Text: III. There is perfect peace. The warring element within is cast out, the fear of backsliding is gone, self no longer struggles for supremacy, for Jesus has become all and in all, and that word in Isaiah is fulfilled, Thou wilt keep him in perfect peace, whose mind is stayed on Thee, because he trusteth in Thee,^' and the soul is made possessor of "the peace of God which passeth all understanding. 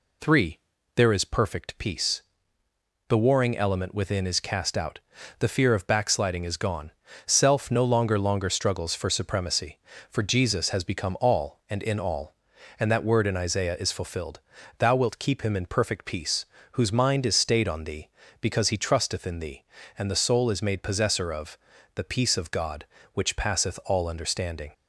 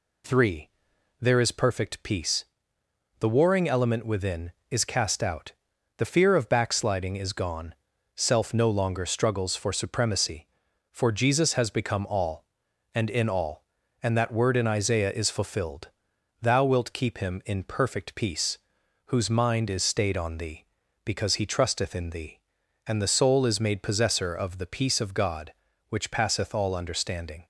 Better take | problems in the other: second | says "longer" twice; at 8.1 s // pauses between "of" and "the"; slight; at 21.5 s; 0.36 s long

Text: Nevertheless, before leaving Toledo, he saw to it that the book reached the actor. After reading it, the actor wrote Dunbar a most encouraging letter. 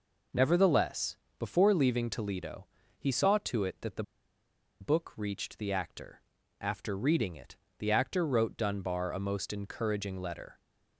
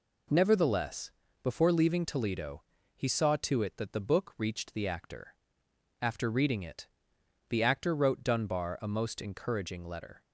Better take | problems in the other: second | pauses between "the" and "book"; noticeable; at 4.0 s; 0.78 s long

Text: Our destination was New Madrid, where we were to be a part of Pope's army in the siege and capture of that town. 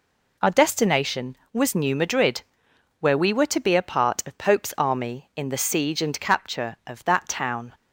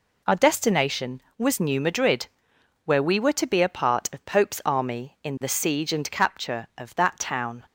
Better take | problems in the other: neither | none

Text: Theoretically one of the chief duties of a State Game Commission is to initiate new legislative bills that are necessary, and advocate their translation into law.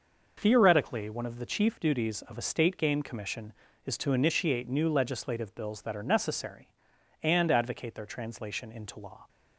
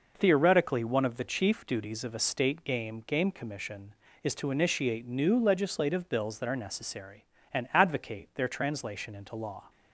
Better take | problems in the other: first | says "Game" twice; at 3.0 s

